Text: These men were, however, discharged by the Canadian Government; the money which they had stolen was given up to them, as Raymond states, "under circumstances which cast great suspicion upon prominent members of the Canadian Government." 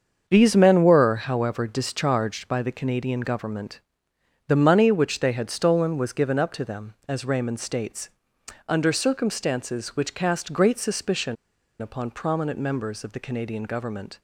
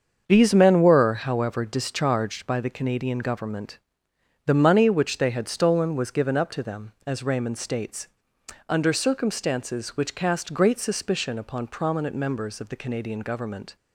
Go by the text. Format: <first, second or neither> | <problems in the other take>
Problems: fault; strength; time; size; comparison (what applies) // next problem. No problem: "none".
second | starts louder than the rest; until 1.2 s; 7 dB; also in the second // pauses between "suspicion" and "upon"; at 11.3 s; 0.45 s long